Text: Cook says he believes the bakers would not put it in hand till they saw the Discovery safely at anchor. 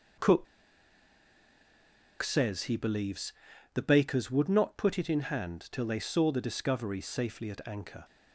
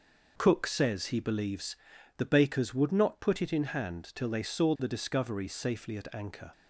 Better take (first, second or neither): second